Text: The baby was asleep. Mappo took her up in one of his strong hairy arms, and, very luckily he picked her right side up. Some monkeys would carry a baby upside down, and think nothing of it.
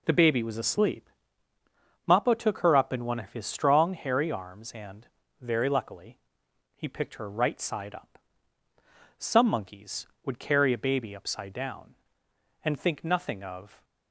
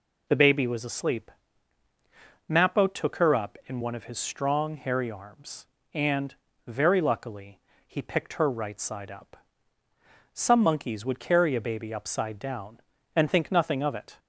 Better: second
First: pauses between "luckily" and "he"; noticeable; at 6.1 s; 0.58 s long // stops before "it"; at 13.8 s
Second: pauses between "luckily" and "he"; slight; at 7.5 s; 0.30 s long

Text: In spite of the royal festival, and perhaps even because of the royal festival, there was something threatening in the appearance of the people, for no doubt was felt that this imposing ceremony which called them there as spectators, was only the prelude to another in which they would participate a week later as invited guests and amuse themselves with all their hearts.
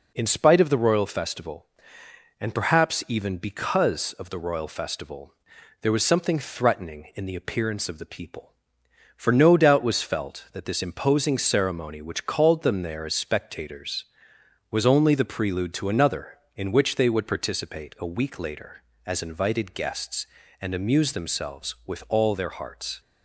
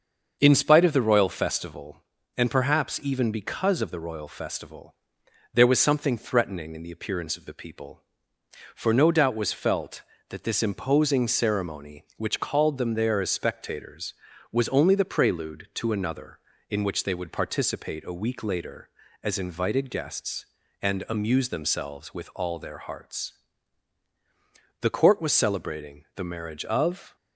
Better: first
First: none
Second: starts louder than the rest; until 1.4 s; 6.5 dB // goes on to say "The court was celebrating the marriage of"; strong; from 24.8 s on; 2.3 s long

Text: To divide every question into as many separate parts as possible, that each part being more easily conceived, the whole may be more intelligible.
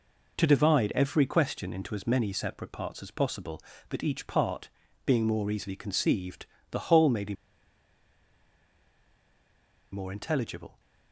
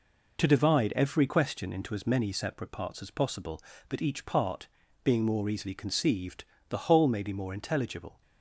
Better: second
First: pauses between "part" and "being"; slight; at 4.7 s; 0.34 s long // pauses between "be" and "more"; strong; at 7.3 s; 2.5 s long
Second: pauses between "part" and "being"; slight; at 4.6 s; 0.34 s long

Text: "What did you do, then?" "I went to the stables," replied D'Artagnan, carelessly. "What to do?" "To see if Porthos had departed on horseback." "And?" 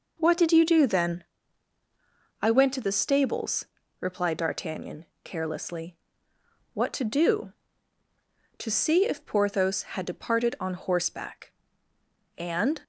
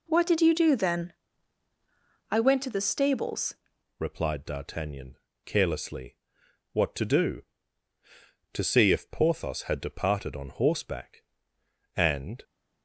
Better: first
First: none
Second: changes voice at "replied"; from 3.9 s on; 8.5 s long

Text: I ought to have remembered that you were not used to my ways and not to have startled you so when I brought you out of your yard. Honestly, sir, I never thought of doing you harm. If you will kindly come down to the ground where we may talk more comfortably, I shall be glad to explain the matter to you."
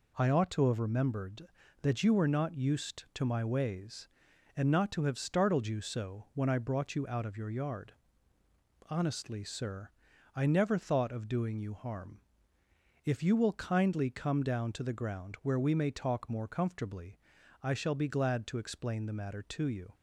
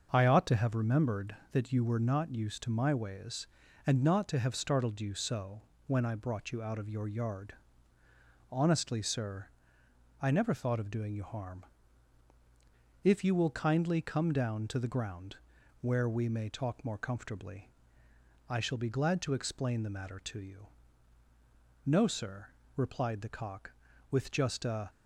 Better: first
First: none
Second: starts louder than the rest; until 1.1 s; 6.5 dB // pauses between "so" and "when"; slight; at 5.6 s; 0.24 s long // pauses between "ground" and "where"; at 15.3 s; 0.44 s long // goes on to say "No sir replied the cock with just a"; strong; from 21.8 s on; 3.0 s long

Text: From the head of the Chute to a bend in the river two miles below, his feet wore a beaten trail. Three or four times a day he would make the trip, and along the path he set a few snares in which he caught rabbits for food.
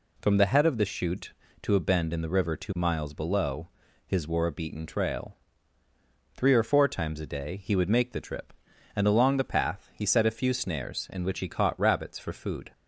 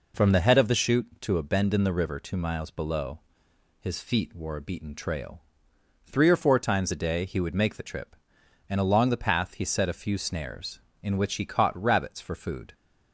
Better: second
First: skips "feet"; at 4.2 s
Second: none

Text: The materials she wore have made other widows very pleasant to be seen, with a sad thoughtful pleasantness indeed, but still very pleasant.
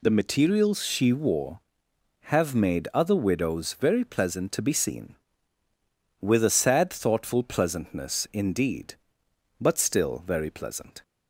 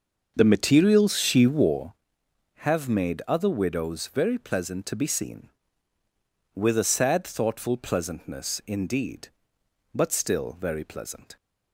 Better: first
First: none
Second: starts louder than the rest; until 2.0 s; 6 dB

